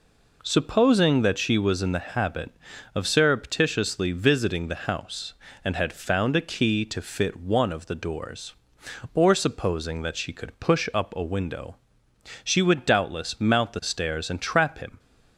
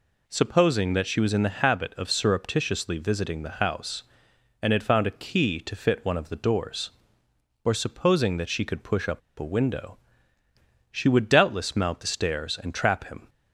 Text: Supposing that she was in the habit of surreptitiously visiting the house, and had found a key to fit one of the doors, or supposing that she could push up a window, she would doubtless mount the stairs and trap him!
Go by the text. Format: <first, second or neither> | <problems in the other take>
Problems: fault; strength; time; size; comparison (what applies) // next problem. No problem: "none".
first | pauses between "up" and "a"; slight; at 9.2 s; 0.18 s long